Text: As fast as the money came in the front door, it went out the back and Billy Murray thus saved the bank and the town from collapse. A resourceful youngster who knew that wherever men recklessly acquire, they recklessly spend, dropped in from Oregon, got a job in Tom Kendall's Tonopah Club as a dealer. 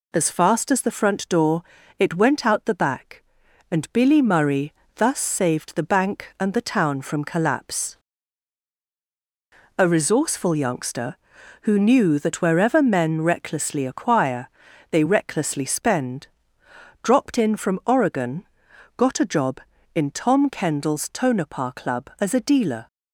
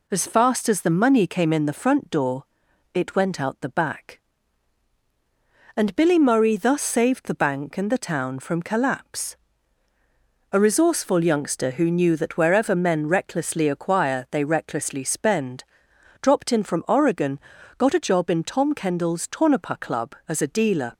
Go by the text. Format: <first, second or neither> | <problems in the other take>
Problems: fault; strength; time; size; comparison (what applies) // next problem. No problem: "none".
second | skips "money came in the"; at 0.9 s // pauses between "Murray" and "thus"; slight; at 4.7 s; 0.22 s long